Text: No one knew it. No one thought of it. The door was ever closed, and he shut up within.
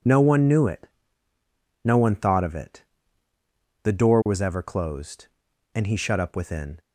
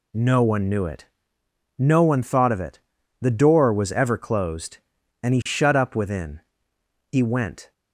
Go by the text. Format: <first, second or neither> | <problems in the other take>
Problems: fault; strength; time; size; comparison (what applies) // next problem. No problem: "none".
first | goes on to say "He went"; noticeable; from 7.0 s on; 0.62 s long